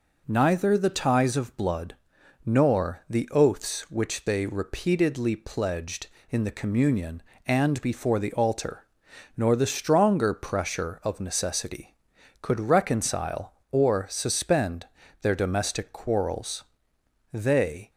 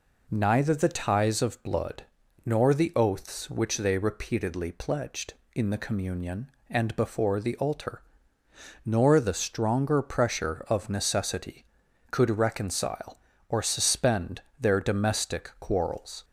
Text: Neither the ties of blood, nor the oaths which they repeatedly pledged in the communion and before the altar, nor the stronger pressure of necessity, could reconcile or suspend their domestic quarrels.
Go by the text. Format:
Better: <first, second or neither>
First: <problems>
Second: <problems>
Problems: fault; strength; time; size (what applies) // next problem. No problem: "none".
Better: second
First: pauses between "suspend" and "their"; slight; at 14.8 s; 0.36 s long // goes on to say "They"; from 17.3 s on; 0.58 s long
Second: pauses between "suspend" and "their"; slight; at 14.4 s; 0.18 s long